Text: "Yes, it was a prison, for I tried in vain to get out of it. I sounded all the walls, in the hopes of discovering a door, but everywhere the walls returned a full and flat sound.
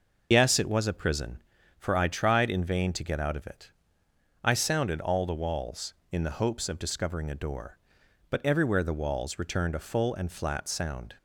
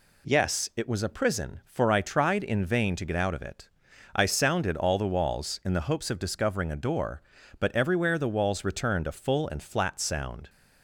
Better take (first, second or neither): second